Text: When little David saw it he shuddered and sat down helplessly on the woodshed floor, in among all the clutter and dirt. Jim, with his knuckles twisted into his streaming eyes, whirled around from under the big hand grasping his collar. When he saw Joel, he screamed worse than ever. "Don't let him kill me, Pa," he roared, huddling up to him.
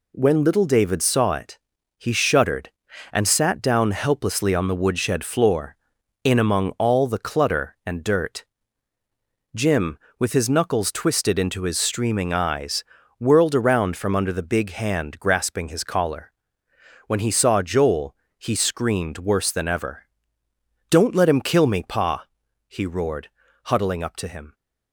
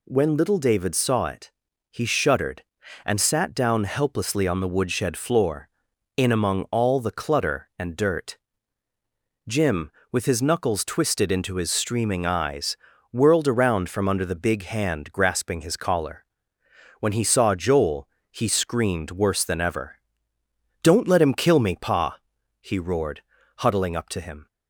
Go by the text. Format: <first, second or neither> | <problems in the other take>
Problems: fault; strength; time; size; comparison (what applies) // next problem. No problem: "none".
second | gets quieter; noticeable; throughout; 6 dB // pauses between "it" and "he"; at 1.5 s; 0.40 s long; also in the second